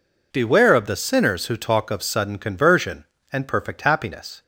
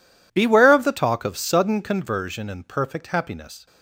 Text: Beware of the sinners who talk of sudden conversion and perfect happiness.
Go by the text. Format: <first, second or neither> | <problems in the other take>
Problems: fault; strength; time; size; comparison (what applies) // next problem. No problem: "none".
first | skips "sinners who"; at 0.9 s